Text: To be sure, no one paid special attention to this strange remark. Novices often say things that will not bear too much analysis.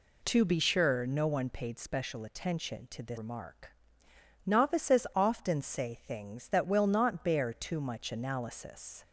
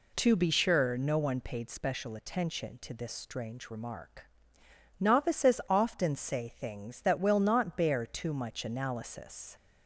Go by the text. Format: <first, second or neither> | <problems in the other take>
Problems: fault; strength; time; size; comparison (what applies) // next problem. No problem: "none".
second | skips "strange"; at 3.1 s